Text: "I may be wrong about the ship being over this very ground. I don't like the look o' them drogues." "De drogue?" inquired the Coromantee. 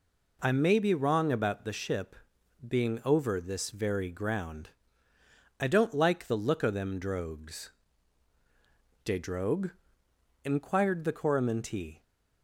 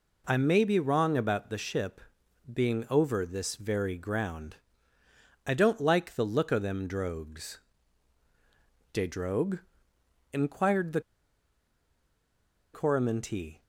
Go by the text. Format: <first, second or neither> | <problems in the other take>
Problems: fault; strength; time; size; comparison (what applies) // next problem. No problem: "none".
first | pauses between "ship" and "being"; noticeable; at 2.0 s; 0.50 s long; noticeable in the first // pauses between "the" and "Coromantee"; strong; at 11.0 s; 1.7 s long